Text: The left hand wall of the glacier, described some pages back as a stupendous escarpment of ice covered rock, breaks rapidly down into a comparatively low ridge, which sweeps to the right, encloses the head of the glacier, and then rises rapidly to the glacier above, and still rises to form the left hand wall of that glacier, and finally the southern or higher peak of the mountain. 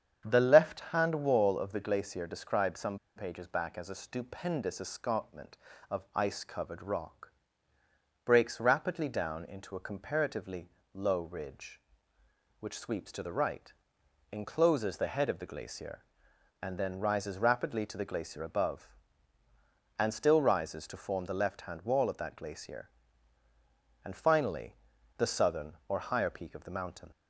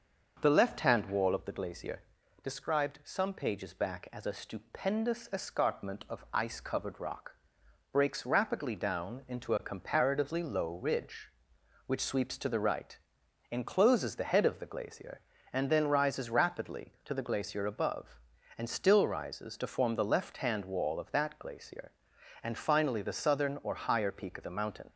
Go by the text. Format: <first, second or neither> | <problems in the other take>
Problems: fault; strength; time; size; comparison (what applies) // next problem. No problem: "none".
second | starts louder than the rest; strong; until 1.2 s; 8 dB; also in the second // pauses between "some" and "pages"; slight; at 2.9 s; 0.18 s long // pauses between "comparatively" and "low"; slight; at 10.6 s; 0.24 s long // pauses between "finally" and "the"; at 24.7 s; 0.42 s long